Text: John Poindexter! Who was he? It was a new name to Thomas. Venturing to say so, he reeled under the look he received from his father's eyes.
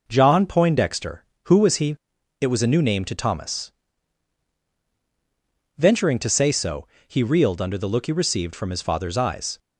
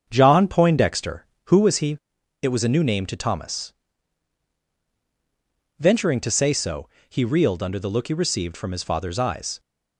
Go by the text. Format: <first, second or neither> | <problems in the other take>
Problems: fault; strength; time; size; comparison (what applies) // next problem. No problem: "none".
first | starts louder than the rest; until 1.7 s; 7 dB